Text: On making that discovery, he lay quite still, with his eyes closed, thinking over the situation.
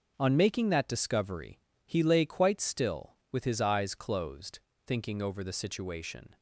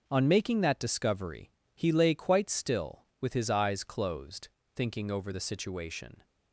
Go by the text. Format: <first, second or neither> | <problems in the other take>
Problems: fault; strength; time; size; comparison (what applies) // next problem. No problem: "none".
neither | none